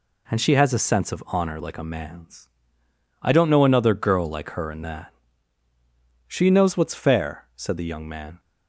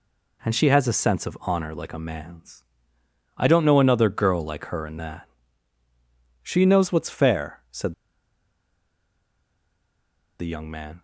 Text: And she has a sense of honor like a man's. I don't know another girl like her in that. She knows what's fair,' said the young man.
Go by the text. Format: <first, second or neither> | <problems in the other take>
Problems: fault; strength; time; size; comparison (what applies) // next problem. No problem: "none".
first | pauses between "said" and "the"; strong; at 7.9 s; 2.4 s long